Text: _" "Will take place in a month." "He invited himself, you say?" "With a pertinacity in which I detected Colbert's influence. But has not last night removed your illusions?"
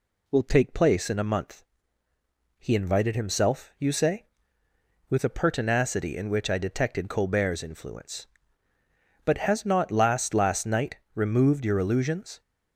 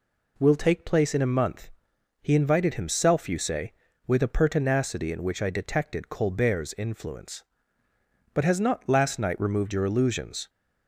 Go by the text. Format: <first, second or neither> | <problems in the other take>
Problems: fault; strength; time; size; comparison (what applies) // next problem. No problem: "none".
second | says "last" twice; at 10.3 s // pauses between "night" and "removed"; slight; at 10.9 s; 0.18 s long